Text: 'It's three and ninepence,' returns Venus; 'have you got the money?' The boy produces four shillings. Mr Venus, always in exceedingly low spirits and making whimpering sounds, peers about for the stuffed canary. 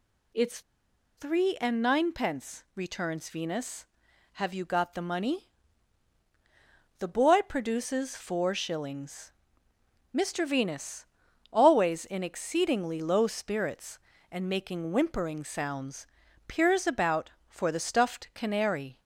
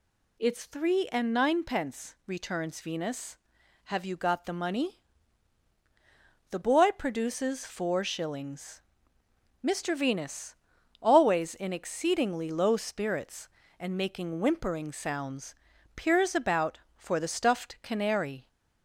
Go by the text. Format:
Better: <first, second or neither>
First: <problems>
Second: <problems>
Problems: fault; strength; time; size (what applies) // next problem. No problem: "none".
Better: second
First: pauses between "It's" and "three"; noticeable; at 0.6 s; 0.56 s long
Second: none